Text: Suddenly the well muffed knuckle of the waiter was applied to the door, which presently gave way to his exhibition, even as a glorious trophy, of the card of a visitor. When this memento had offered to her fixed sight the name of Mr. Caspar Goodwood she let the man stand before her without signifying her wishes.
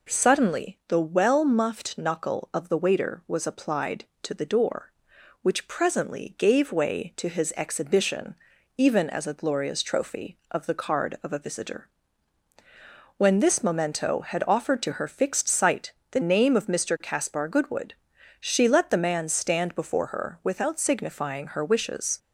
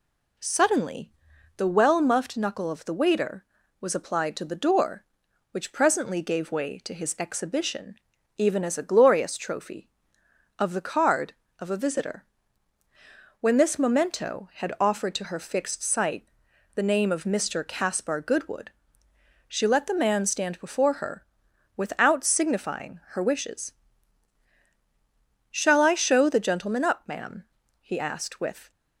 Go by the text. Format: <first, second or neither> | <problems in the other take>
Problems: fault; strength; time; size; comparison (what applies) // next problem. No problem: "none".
first | pauses between "Suddenly" and "the"; noticeable; at 1.1 s; 0.46 s long // pauses between "sight" and "the"; noticeable; at 16.2 s; 0.48 s long; slight in the first // pauses between "Goodwood" and "she"; noticeable; at 18.7 s; 0.78 s long; noticeable in the first // pauses between "her" and "without"; noticeable; at 21.2 s; 0.52 s long // goes on to say "Shall I show the gentleman up ma'am he asked with"; strong; from 25.4 s on; 3.2 s long